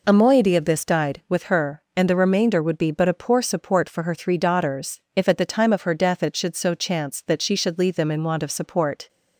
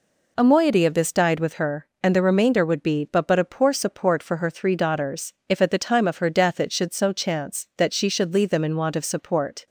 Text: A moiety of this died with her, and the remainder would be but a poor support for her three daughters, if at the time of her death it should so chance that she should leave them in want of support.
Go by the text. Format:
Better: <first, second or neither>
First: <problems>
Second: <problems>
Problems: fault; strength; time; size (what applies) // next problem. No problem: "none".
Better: first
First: none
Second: says "but" twice; at 3.2 s